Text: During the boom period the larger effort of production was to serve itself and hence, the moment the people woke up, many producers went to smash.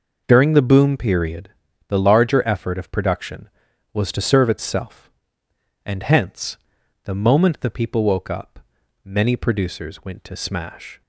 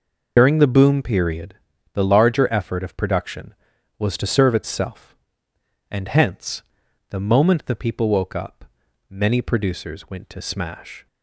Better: first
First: pauses between "period" and "the"; at 1.4 s; 0.40 s long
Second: loses the start of "During"; at 0.3 s; 60 ms // pauses between "period" and "the"; at 1.5 s; 0.40 s long

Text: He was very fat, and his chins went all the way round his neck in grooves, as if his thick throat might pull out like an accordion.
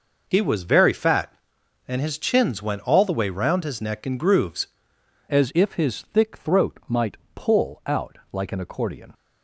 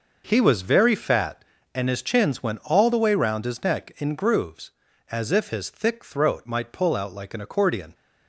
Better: second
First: changes voice at "as"; from 5.2 s on; 3.9 s long // pauses between "might" and "pull"; slight; at 7.1 s; 0.16 s long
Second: none

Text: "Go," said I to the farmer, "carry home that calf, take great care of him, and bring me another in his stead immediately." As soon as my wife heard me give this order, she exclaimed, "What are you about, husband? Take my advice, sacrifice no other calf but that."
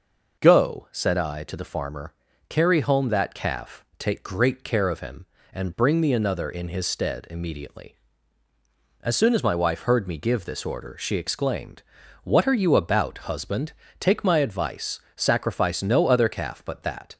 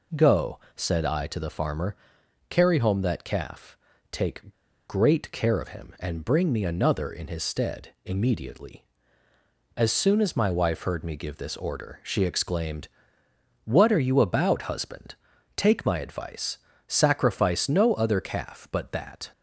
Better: first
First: none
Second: pauses between "take" and "great"; slight; at 4.5 s; 0.34 s long

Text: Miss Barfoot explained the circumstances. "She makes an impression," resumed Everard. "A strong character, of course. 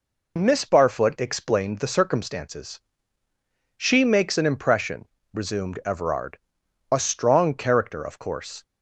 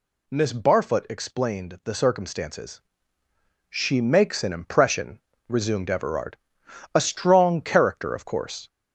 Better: first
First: none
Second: gets louder; throughout; 3.5 dB

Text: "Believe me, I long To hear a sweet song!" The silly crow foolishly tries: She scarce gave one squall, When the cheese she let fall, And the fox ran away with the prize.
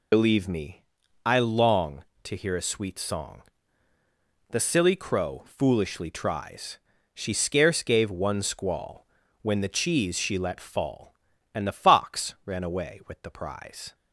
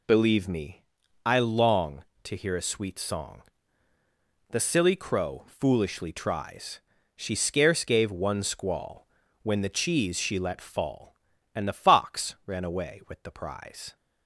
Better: second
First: loses the start of "Believe"; at 0.1 s; 60 ms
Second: none

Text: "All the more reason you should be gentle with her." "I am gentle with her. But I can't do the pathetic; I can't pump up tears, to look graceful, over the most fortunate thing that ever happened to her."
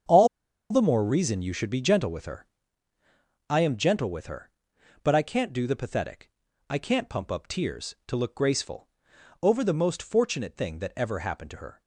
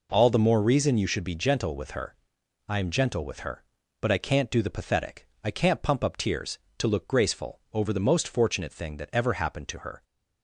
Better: second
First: starts louder than the rest; strong; until 1.5 s; 7.5 dB // pauses between "All" and "the"; at 0.2 s; 0.44 s long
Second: none

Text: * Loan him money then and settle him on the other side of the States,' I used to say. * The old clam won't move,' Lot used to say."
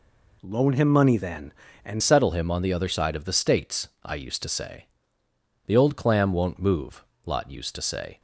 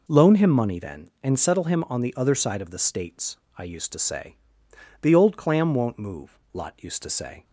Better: second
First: changes voice at "settle"; from 2.0 s on; 6.1 s long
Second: none

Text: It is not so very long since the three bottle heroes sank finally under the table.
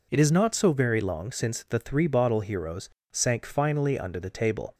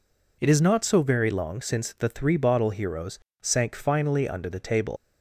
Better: first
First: pauses between "heroes" and "sank"; slight; at 2.8 s; 0.24 s long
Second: pauses between "heroes" and "sank"; slight; at 3.1 s; 0.24 s long // leaves "table" unfinished; at 4.9 s; 80 ms

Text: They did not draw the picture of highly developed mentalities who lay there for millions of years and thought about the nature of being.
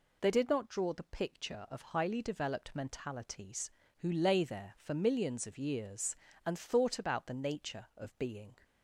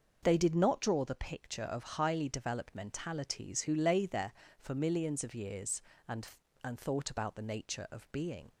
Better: first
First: none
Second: starts louder than the rest; noticeable; until 1.2 s; 6 dB // says "and" twice; at 6.6 s

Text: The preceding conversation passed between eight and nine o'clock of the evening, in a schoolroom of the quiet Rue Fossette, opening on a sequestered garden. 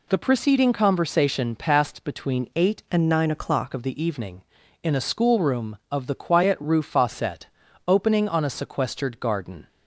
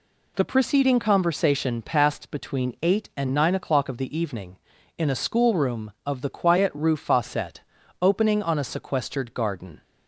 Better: second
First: changes voice from "and" to "o'clock"; from 2.9 to 3.7 s; 0.8 s long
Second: none

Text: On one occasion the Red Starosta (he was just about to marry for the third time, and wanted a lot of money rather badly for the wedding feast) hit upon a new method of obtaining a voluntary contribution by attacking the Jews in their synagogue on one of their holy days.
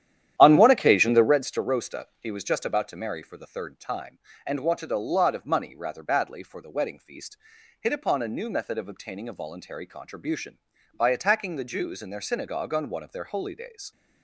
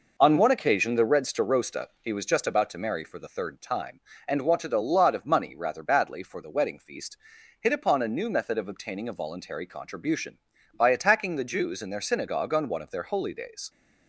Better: second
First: starts louder than the rest; strong; until 1.5 s; 11 dB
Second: none

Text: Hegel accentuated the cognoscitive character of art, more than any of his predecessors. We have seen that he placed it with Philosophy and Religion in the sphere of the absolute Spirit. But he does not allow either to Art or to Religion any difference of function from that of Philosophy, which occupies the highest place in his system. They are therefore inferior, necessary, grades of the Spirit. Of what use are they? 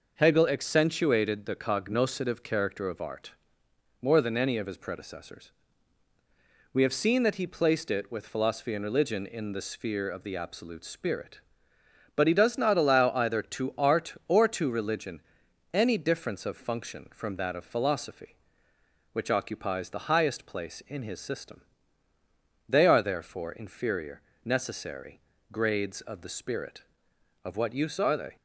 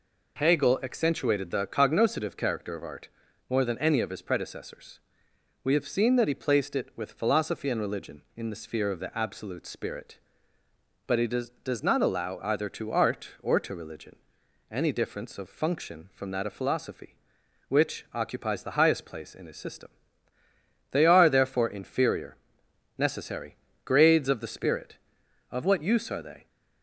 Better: first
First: pauses between "Religion" and "any"; noticeable; at 15.1 s; 0.52 s long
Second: says "does" twice; at 11.6 s // pauses between "Religion" and "any"; noticeable; at 14.1 s; 0.52 s long

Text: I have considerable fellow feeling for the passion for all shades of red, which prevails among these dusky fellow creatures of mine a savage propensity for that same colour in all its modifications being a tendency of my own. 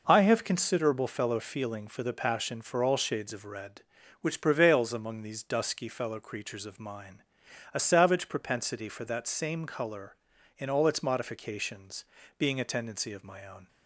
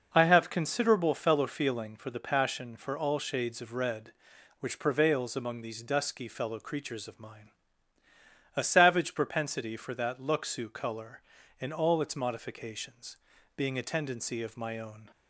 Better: first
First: pauses between "mine" and "a"; noticeable; at 7.2 s; 0.50 s long // pauses between "modifications" and "being"; slight; at 12.0 s; 0.34 s long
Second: pauses between "mine" and "a"; at 7.5 s; 1.0 s long // says "luxu" for "same"; at 10.1 s // pauses between "modifications" and "being"; slight; at 13.1 s; 0.36 s long

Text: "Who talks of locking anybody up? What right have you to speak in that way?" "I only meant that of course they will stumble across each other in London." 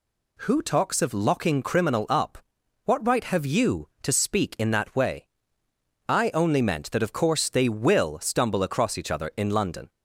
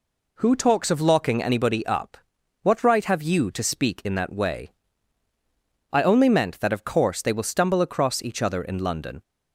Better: second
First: says "criminal" for "anybody"; at 1.6 s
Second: none

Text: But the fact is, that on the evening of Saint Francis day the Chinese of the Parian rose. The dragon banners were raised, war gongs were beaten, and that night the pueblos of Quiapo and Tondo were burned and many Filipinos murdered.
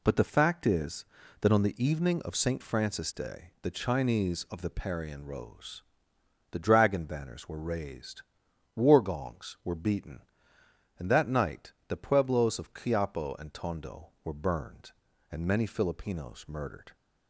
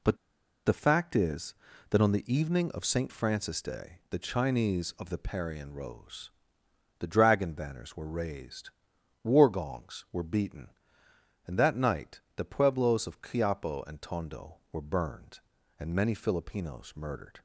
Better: first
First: pauses between "night" and "the"; slight; at 11.7 s; 0.16 s long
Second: pauses between "But" and "the"; noticeable; at 0.1 s; 0.50 s long // pauses between "night" and "the"; slight; at 12.2 s; 0.16 s long

